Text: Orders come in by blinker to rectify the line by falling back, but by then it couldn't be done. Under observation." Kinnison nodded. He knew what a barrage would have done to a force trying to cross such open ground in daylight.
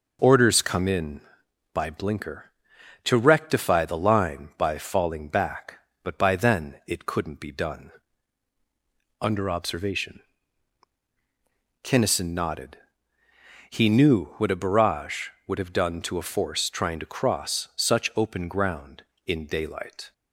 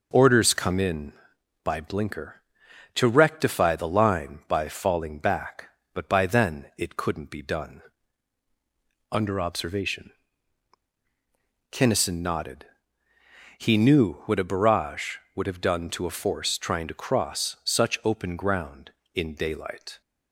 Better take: neither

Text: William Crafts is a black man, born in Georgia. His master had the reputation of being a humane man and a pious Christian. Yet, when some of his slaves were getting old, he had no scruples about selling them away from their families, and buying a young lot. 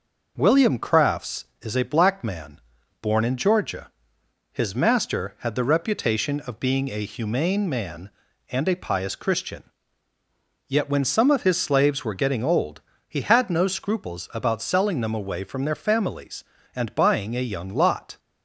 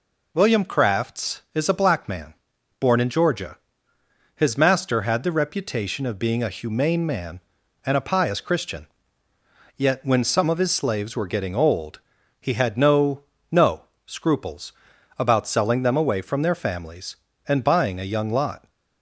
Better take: first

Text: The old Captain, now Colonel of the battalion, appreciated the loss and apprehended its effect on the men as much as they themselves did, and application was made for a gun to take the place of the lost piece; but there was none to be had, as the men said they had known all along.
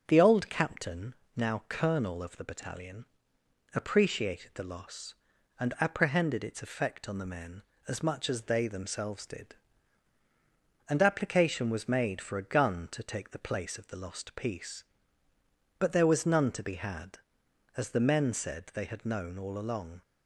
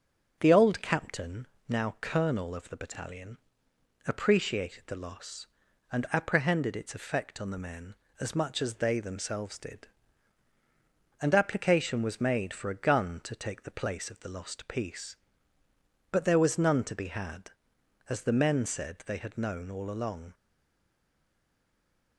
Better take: first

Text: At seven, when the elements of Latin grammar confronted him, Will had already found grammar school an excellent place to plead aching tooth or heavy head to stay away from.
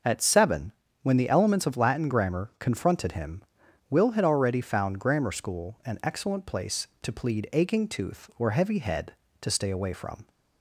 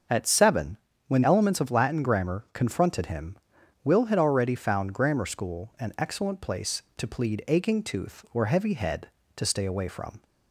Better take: first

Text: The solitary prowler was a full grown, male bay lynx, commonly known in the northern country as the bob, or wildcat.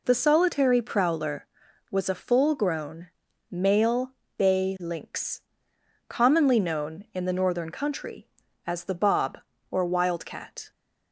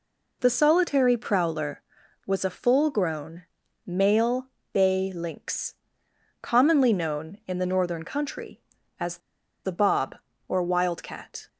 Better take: first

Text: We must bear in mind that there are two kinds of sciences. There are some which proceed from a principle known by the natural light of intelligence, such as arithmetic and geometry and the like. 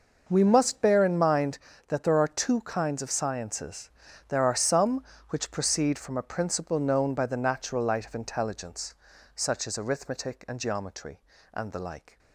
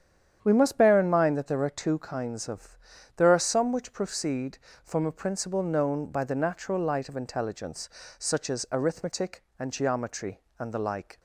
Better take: first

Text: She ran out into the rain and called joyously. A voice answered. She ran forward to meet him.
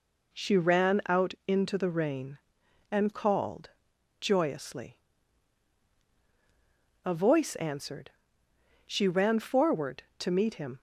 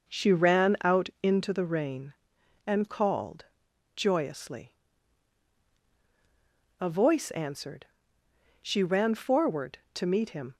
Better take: first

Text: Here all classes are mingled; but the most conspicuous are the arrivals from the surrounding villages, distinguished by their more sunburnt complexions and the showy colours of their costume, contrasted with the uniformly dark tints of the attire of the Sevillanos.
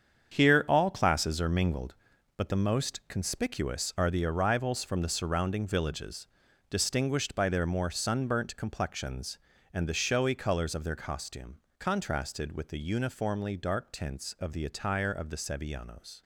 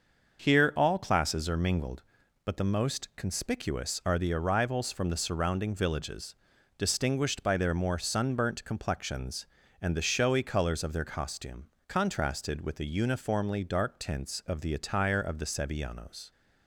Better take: second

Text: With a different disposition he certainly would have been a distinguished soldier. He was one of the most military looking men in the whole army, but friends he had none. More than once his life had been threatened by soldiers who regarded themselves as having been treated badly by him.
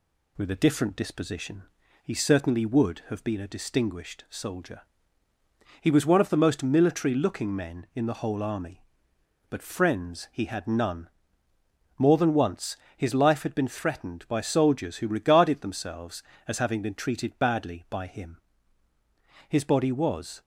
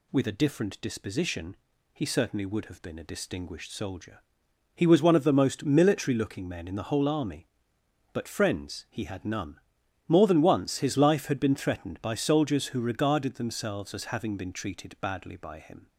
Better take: second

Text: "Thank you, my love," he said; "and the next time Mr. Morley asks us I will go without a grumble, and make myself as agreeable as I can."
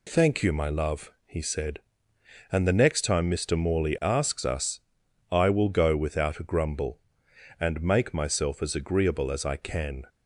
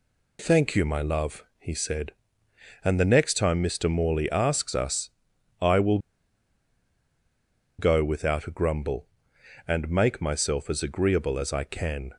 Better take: first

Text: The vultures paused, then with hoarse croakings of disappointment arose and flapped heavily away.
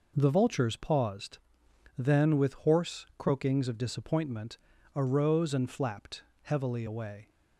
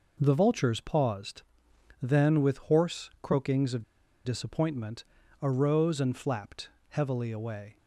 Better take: first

